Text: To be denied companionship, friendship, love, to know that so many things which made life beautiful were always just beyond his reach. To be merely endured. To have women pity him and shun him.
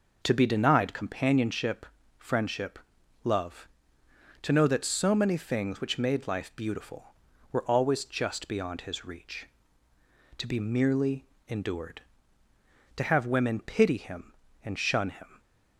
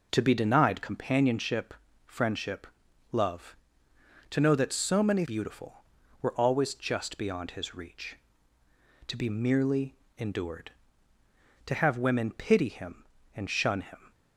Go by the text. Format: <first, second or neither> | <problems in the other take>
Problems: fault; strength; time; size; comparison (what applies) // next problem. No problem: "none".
first | skips "things which made life"; at 5.2 s // pauses between "merely" and "endured"; slight; at 9.9 s; 0.22 s long; slight in the first